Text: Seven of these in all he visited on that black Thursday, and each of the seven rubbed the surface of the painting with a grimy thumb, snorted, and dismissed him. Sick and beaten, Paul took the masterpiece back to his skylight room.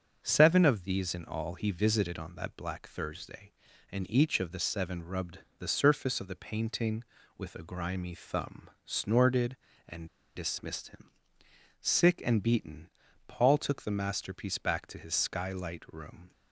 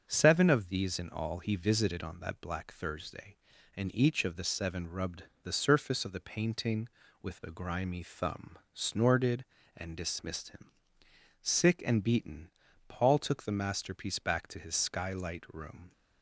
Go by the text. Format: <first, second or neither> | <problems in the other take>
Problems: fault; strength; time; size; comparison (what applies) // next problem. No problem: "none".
second | starts louder than the rest; until 1.2 s; 6.5 dB; also in the second // pauses between "rubbed" and "the"; slight; at 5.3 s; 0.18 s long; slight in the second // pauses between "and" and "dismissed"; slight; at 10.0 s; 0.28 s long